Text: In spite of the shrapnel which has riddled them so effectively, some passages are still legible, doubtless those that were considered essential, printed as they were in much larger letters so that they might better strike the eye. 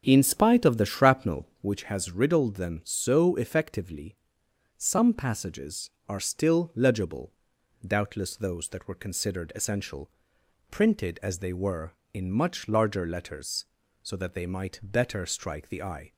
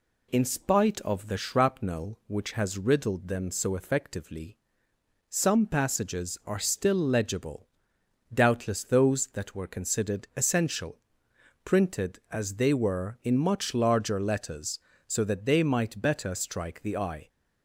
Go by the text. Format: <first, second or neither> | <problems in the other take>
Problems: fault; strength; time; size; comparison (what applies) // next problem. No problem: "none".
second | starts louder than the rest; until 1.9 s; 7 dB